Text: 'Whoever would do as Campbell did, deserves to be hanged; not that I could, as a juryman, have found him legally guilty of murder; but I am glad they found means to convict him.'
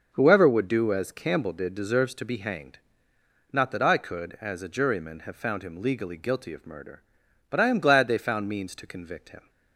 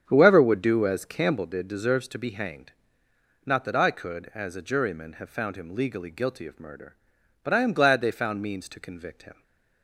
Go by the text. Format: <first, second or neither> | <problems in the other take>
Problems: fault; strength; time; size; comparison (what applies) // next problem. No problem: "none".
first | starts louder than the rest; strong; until 1.4 s; 8 dB // stays silent after the last word; slight; from 9.3 s on; 0.5 s long